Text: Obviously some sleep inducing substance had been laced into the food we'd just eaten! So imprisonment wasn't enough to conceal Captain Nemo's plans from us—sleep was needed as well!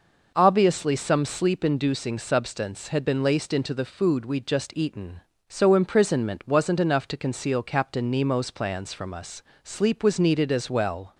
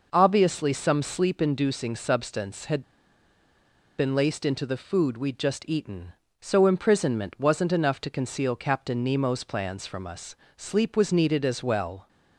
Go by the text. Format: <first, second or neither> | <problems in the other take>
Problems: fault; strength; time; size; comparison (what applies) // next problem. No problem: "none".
first | pauses between "had" and "been"; at 2.8 s; 1.1 s long